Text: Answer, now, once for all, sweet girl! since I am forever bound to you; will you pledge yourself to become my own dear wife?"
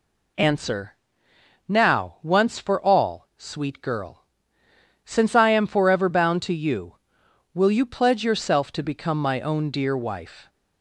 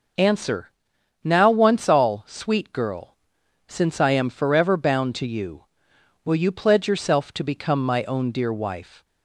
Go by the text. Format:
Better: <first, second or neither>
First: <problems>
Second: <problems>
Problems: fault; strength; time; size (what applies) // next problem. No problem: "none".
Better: first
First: none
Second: skips "for"; at 1.8 s